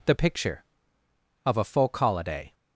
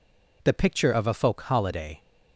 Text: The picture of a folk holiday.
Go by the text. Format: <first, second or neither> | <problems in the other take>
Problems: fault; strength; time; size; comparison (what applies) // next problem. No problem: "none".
neither | none